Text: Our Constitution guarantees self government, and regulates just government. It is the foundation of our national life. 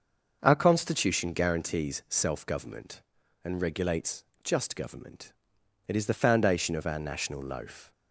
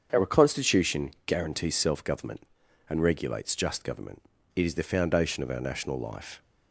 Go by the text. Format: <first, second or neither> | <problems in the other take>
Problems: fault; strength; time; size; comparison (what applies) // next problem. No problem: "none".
second | starts louder than the rest; until 1.4 s; 6.5 dB; strong in the second // pauses between "regulates" and "just"; slight; at 4.2 s; 0.18 s long // says "loaf" for "life"; at 7.4 s